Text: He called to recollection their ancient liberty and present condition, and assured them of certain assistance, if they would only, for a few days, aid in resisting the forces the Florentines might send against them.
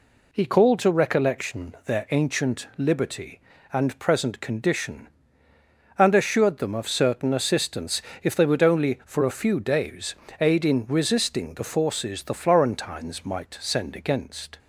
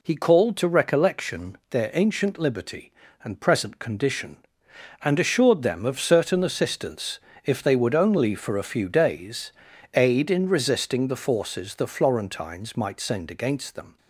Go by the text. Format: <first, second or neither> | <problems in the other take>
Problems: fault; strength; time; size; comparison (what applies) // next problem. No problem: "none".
second | stops before "them"; at 14.5 s